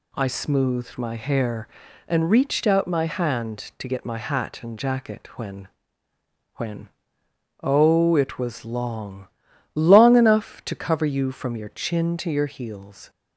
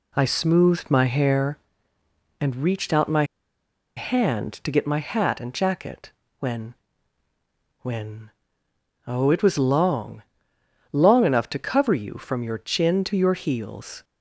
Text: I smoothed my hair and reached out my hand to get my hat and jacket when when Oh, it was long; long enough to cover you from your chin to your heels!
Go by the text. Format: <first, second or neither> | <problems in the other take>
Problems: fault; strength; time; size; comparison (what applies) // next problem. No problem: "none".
first | pauses between "my" and "hand"; noticeable; at 3.2 s; 0.73 s long // pauses between "jacket" and "when"; slight; at 6.1 s; 0.28 s long // pauses between "when" and "when"; at 6.7 s; 1.0 s long; noticeable in the first // pauses between "when" and "Oh"; noticeable; at 8.2 s; 0.76 s long; noticeable in the first